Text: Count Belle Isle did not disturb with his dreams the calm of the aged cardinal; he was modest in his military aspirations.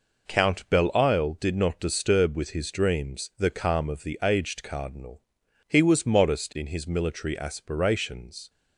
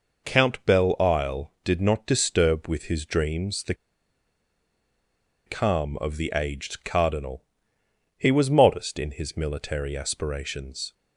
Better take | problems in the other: first | pauses between "the" and "calm"; strong; at 3.7 s; 1.7 s long

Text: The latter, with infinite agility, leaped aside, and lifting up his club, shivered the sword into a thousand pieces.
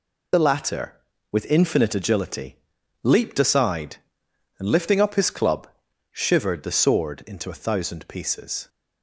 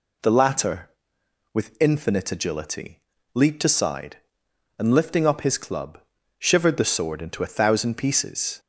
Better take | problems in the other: second | loses the start of "The"; at 0.3 s; 30 ms

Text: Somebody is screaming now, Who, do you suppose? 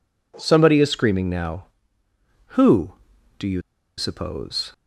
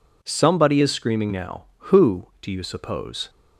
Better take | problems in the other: second | pauses between "you" and "suppose"; at 3.6 s; 0.37 s long

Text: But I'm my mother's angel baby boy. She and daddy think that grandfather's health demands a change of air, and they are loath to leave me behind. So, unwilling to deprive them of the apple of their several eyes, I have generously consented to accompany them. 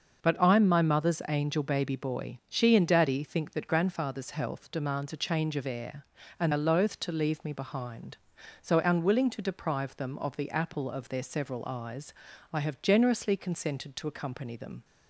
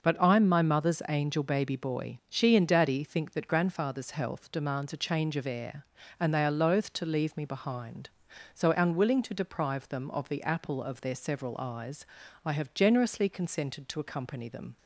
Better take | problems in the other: second | starts louder than the rest; until 1.2 s; 6 dB // skips "they"; at 6.5 s

